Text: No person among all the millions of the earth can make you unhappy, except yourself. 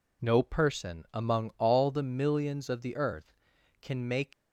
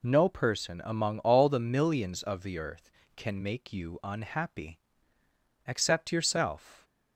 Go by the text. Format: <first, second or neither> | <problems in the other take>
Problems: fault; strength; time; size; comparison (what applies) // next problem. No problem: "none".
second | stops before "you unhappy except yourself"; at 4.3 s